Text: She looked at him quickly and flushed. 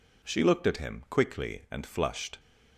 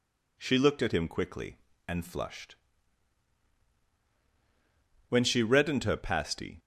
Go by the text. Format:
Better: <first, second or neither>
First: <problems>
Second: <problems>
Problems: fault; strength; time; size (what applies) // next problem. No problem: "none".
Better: first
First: none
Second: goes on to say "When she reddened her pasty"; from 5.0 s on; 1.5 s long